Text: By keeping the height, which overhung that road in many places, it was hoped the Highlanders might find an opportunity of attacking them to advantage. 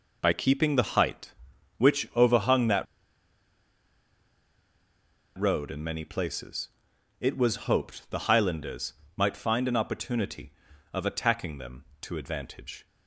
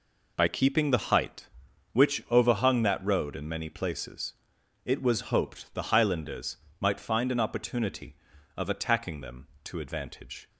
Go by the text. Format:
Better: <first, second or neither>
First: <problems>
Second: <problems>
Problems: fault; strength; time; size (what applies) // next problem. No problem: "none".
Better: second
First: pauses between "that" and "road"; strong; at 2.8 s; 2.5 s long // pauses between "Highlanders" and "might"; slight; at 8.9 s; 0.24 s long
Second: pauses between "Highlanders" and "might"; slight; at 6.5 s; 0.24 s long